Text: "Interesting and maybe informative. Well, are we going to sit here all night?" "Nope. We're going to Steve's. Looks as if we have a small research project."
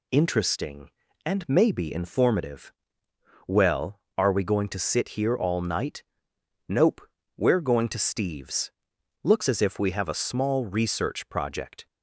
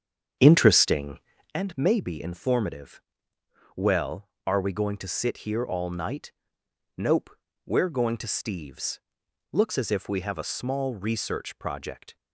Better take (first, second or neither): first